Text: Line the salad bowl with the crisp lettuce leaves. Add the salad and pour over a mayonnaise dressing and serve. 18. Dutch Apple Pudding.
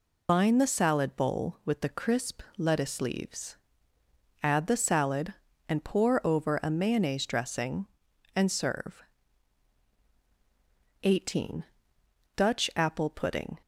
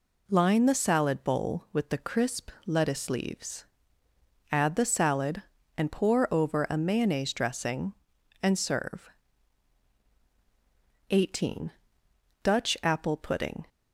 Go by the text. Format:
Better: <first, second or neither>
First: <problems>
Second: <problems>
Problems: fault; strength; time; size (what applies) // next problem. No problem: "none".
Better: second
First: loses the start of "Line"; at 0.2 s; 90 ms // pauses between "crisp" and "lettuce"; slight; at 2.4 s; 0.16 s long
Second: pauses between "crisp" and "lettuce"; slight; at 2.4 s; 0.16 s long